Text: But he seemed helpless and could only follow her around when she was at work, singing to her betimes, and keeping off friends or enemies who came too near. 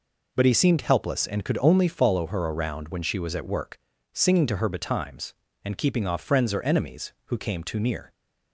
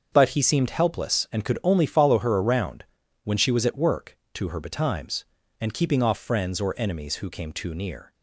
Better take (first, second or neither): first